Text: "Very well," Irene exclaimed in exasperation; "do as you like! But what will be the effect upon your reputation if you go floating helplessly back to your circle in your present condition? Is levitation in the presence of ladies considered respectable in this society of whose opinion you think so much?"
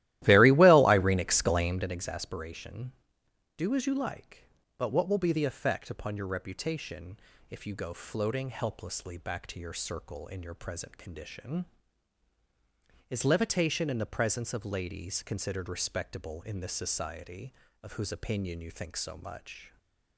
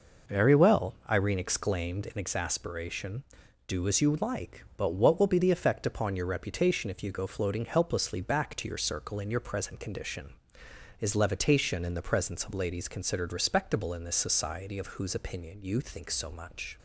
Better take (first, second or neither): second